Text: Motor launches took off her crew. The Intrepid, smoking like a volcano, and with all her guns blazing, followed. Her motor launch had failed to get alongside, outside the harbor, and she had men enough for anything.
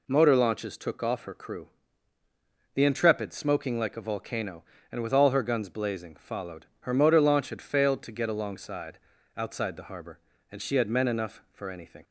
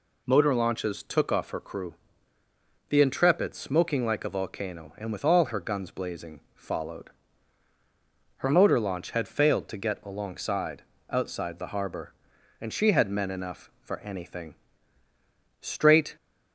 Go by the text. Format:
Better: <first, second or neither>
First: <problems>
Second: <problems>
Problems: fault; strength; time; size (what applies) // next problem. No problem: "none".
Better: first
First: none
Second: goes on to say "Straight"; from 15.5 s on; 0.56 s long